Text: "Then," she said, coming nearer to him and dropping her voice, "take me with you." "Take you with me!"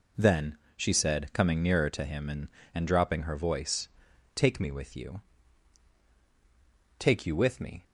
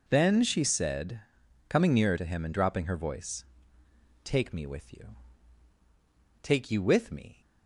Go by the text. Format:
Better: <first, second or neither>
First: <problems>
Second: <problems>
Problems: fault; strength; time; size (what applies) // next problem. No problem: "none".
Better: second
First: says "and" twice; at 2.7 s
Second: none